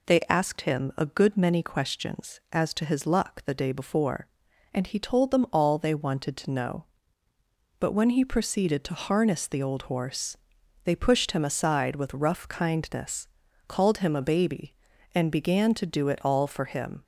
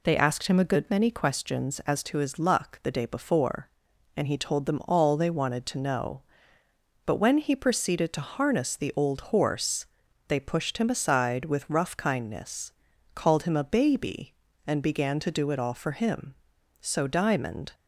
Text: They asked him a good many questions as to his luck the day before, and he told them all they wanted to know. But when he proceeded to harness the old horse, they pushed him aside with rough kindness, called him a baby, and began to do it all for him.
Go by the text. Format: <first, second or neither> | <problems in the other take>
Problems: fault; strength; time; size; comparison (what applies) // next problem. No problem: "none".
first | goes on to say "So Diamond"; noticeable; from 16.8 s on; 0.92 s long